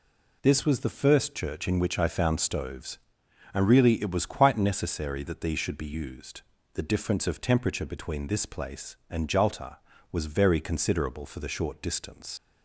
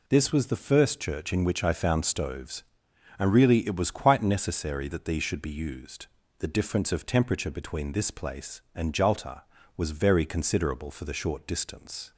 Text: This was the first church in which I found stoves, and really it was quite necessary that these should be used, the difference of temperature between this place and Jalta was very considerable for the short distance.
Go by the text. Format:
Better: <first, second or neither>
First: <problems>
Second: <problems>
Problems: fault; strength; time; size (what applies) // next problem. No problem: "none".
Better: second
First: leaves "distance" unfinished; at 12.3 s; 110 ms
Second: none